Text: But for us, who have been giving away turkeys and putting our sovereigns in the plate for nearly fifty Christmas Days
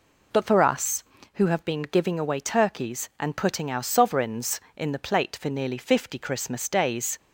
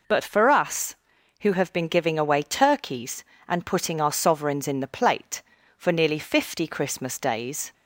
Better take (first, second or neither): neither